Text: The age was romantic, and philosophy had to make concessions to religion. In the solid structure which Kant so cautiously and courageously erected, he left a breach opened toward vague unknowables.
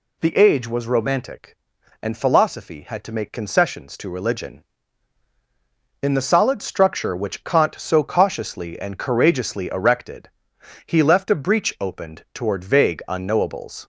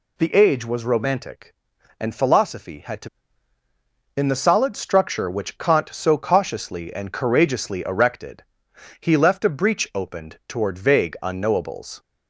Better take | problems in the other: first | skips "make concessions to religion"; at 3.6 s

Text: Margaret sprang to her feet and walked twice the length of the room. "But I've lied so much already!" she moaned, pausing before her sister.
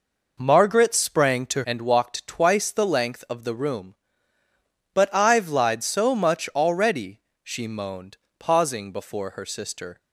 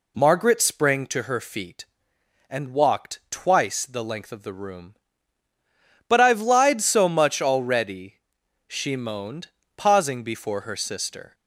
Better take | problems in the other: second | skips "her feet"; at 1.6 s

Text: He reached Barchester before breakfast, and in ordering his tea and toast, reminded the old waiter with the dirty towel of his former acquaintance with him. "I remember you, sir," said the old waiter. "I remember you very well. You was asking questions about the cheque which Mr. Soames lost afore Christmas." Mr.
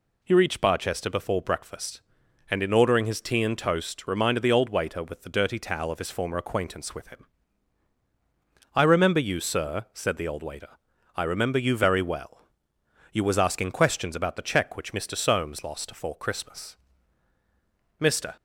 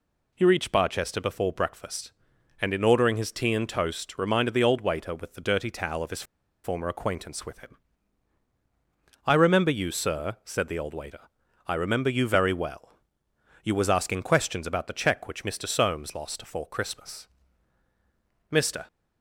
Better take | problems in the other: first | pauses between "his" and "former"; at 6.2 s; 0.41 s long

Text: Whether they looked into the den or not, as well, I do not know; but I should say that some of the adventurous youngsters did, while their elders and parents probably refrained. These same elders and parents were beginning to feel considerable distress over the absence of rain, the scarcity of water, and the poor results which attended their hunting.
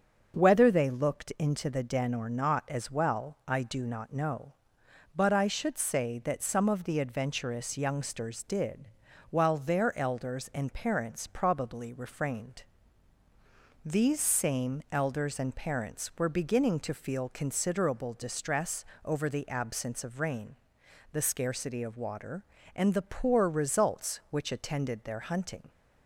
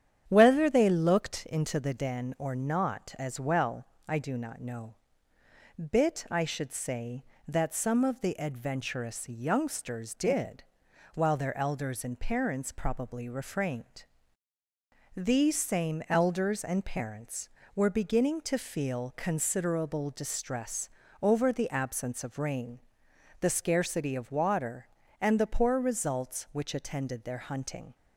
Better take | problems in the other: first | starts louder than the rest; strong; until 1.2 s; 9 dB; also in the first // says "bit" for "but"; at 5.7 s // pauses between "distress" and "over"; slight; at 20.8 s; 0.34 s long; slight in the first

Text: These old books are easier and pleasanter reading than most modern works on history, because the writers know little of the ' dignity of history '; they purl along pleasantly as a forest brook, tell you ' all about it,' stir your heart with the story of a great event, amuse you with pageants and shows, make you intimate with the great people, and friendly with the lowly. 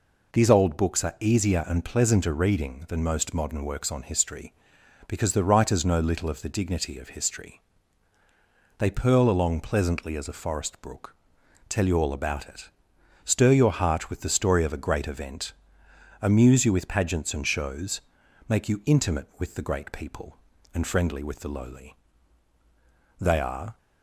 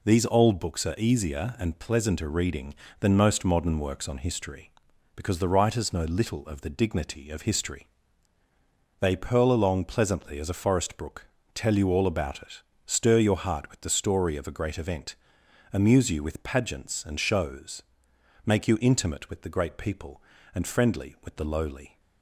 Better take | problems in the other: second | goes on to say "They are"; from 23.1 s on; 0.60 s long

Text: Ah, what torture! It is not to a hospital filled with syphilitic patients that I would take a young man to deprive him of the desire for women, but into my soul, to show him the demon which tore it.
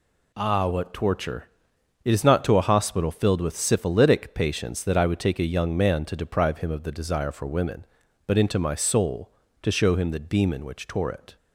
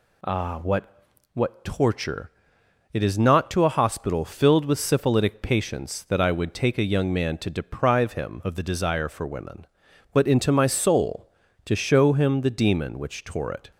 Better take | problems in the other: first | says "what" twice; at 1.3 s

